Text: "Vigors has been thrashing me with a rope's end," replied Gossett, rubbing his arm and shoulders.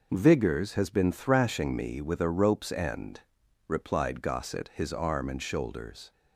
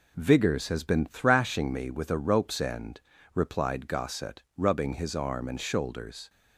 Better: second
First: skips "rubbing"; at 4.7 s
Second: none

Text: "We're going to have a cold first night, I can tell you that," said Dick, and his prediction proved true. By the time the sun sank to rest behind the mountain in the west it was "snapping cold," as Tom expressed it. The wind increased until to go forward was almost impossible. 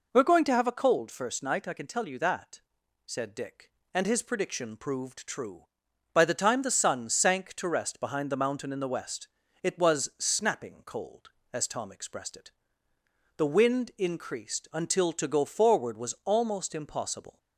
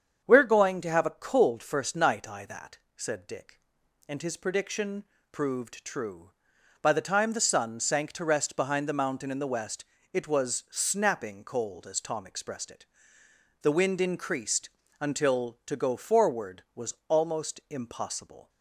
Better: first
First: pauses between "west" and "it"; slight; at 9.2 s; 0.34 s long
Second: starts louder than the rest; strong; until 1.2 s; 7.5 dB // skips "can tell you"; at 2.4 s // pauses between "prediction" and "proved"; slight; at 5.0 s; 0.30 s long // pauses between "west" and "it"; slight; at 9.8 s; 0.30 s long // pauses between "increased" and "until"; slight; at 14.6 s; 0.32 s long

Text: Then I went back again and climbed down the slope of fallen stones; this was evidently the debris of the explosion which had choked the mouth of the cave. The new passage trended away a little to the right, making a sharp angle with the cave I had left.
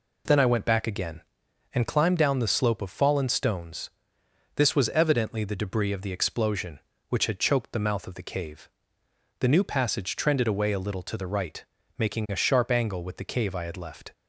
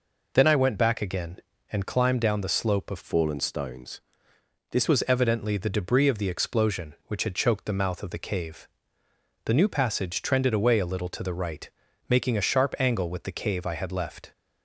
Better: first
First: none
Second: changes voice from "fallen" to "this"; from 3.0 to 4.8 s; 1.8 s long

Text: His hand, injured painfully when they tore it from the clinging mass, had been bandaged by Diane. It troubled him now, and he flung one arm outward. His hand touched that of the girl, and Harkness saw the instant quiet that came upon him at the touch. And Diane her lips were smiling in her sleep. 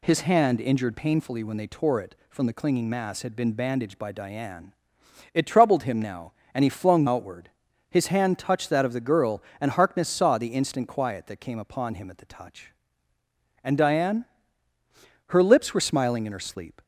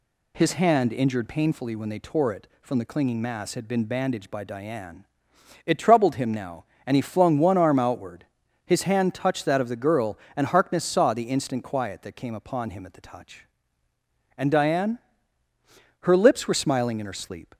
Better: second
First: skips "one arm"; at 7.0 s // pauses between "Diane" and "her"; at 14.2 s; 1.0 s long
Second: pauses between "Diane" and "her"; at 14.9 s; 1.0 s long

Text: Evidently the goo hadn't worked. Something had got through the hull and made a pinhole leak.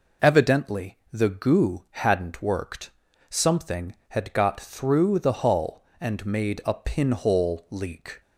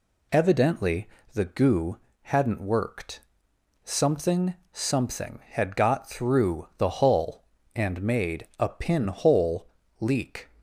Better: first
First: none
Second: pauses between "Evidently" and "the"; slight; at 1.0 s; 0.26 s long // pauses between "goo" and "hadn't"; slight; at 1.9 s; 0.26 s long // says "Something" twice; at 4.7 s // pauses between "pinhole" and "leak"; slight; at 9.6 s; 0.34 s long

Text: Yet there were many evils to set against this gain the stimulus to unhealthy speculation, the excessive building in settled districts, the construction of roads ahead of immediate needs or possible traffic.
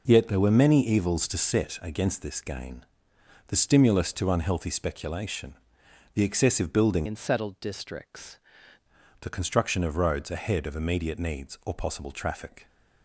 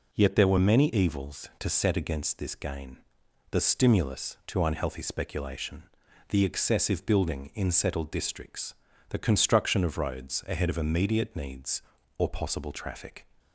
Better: second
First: pauses between "gain" and "the"; noticeable; at 2.8 s; 0.62 s long // changes voice from "in" to "districts"; from 7.0 to 8.3 s; 1.3 s long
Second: pauses between "gain" and "the"; noticeable; at 2.9 s; 0.54 s long

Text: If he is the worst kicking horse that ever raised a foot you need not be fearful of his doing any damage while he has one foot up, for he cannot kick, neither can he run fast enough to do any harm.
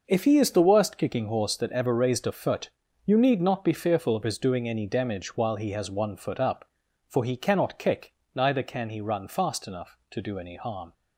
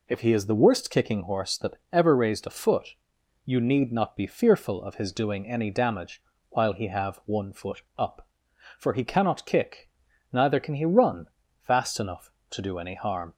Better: first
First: pauses between "foot" and "you"; slight; at 2.6 s; 0.36 s long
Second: pauses between "foot" and "you"; noticeable; at 2.9 s; 0.52 s long // pauses between "damage" and "while"; slight; at 6.2 s; 0.28 s long // says "have" for "has"; at 6.8 s // pauses between "foot" and "up"; slight; at 7.8 s; 0.16 s long // pauses between "run" and "fast"; at 11.2 s; 0.40 s long

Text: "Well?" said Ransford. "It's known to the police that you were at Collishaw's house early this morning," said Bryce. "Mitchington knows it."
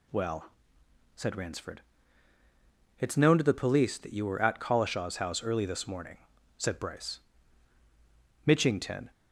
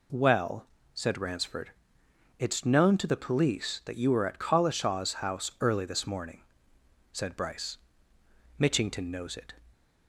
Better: second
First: stops before "knows it"; at 9.1 s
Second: none

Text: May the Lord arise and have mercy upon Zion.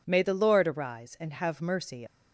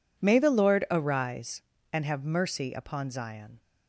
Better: second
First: stops before "upon Zion"; at 2.0 s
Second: none

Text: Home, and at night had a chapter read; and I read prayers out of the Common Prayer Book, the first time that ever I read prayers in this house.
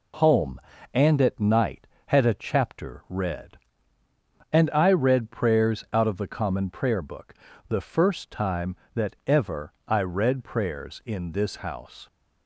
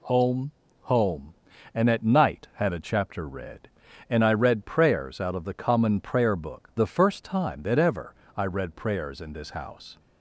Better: first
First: pauses between "ever" and "I"; slight; at 9.7 s; 0.16 s long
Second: says "Home" twice; at 0.8 s // pauses between "ever" and "I"; slight; at 8.1 s; 0.20 s long

